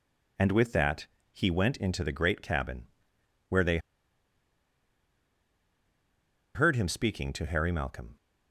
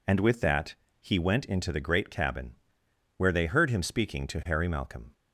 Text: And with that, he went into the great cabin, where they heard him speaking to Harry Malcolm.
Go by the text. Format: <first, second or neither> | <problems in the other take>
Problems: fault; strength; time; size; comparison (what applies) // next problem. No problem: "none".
second | pauses between "they" and "heard"; strong; at 3.7 s; 2.7 s long